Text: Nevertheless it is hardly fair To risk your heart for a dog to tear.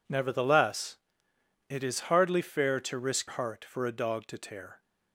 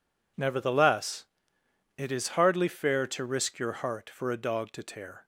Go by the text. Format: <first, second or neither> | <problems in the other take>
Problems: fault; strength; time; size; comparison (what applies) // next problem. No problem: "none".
second | pauses between "Nevertheless" and "it"; noticeable; at 0.9 s; 0.70 s long; noticeable in the second // skips "your"; at 3.2 s